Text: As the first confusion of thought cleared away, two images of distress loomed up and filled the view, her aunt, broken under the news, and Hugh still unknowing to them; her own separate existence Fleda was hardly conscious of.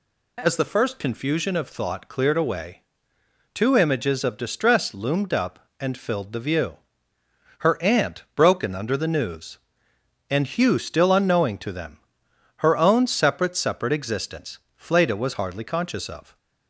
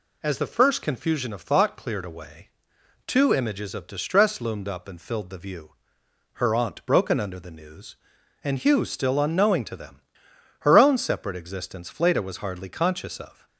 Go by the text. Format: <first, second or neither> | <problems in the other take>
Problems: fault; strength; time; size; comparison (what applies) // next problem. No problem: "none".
second | says "separate" twice; at 13.5 s // pauses between "existence" and "Fleda"; slight; at 14.5 s; 0.18 s long